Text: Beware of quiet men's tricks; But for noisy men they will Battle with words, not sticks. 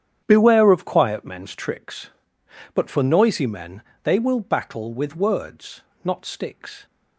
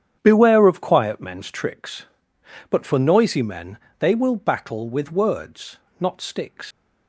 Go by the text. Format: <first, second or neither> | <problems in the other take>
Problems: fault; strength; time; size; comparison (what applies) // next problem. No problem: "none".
first | starts louder than the rest; strong; until 1.2 s; 9 dB; strong in the first // pauses between "men" and "they"; slight; at 3.7 s; 0.24 s long; slight in the first // leaves "sticks" unfinished; at 6.7 s; 100 ms